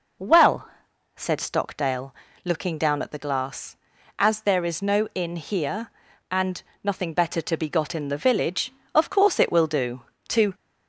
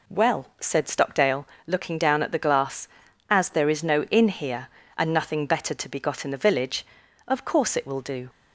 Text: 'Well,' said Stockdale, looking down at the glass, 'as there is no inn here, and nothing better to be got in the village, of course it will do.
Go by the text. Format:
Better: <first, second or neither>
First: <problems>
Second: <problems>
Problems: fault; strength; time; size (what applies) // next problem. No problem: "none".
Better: second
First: pauses between "and" and "nothing"; slight; at 6.6 s; 0.22 s long // goes on to say "To"; slight; from 10.3 s on; 0.24 s long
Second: none